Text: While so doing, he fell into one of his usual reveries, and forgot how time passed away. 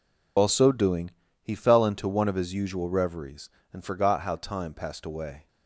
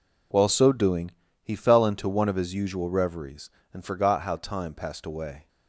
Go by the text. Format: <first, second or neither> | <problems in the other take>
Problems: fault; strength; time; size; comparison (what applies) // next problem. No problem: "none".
second | loses the start of "While"; at 0.3 s; 65 ms